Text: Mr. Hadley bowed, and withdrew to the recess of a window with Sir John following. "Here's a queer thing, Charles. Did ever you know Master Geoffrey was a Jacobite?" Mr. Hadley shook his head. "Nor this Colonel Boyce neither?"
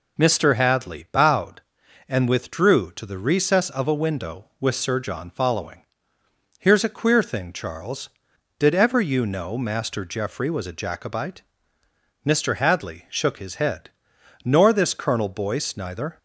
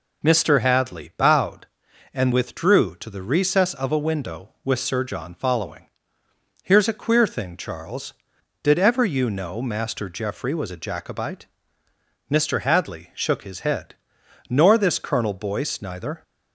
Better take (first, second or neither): neither